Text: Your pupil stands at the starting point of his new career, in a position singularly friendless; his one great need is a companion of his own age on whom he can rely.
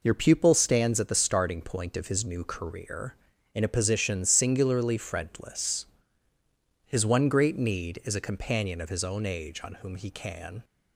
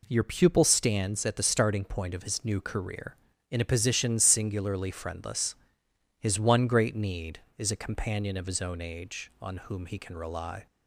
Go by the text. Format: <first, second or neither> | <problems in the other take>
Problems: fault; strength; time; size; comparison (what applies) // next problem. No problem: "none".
second | stops before "rely"; at 10.6 s